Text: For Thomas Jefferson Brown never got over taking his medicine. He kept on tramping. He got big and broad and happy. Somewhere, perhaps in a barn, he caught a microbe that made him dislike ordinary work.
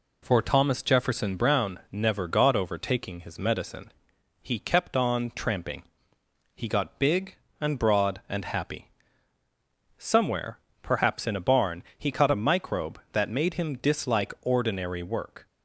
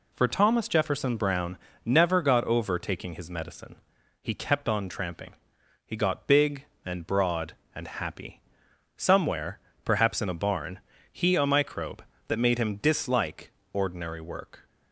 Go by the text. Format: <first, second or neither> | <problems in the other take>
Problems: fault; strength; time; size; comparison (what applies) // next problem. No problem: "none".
first | pauses between "Brown" and "never"; slight; at 1.5 s; 0.26 s long // skips "caught"; at 11.3 s // pauses between "dislike" and "ordinary"; slight; at 13.5 s; 0.22 s long